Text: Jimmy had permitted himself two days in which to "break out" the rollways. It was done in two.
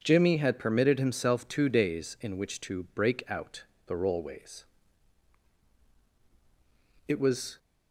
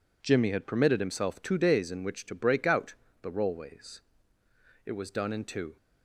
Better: second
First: pauses between "out" and "the"; slight; at 3.6 s; 0.22 s long // stops before "done in two"; at 7.5 s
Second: pauses between "out" and "the"; slight; at 2.9 s; 0.28 s long

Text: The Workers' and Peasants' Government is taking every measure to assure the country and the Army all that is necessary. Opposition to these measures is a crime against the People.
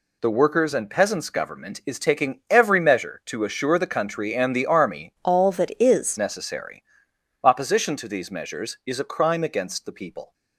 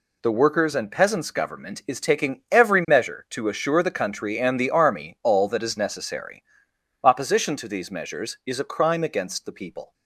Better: second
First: changes voice from "all" to "is"; from 5.2 to 6.1 s; 0.9 s long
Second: none

